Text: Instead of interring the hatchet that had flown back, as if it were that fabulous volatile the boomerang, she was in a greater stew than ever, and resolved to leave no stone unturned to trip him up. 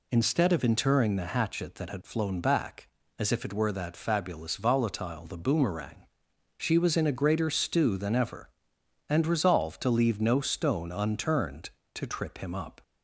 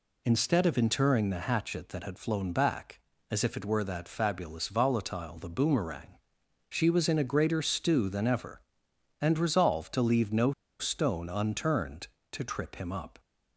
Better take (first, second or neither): first